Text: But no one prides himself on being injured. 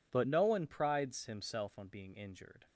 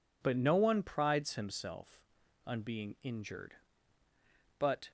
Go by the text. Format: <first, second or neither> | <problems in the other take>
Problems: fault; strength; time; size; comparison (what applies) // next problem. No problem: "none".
first | goes on to say "But"; slight; from 4.5 s on; 0.32 s long